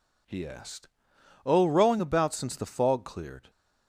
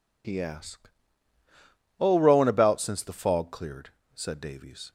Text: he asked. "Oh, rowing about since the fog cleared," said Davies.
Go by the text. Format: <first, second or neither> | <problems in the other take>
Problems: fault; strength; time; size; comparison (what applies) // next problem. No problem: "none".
second | stops before "said Davies"; at 3.4 s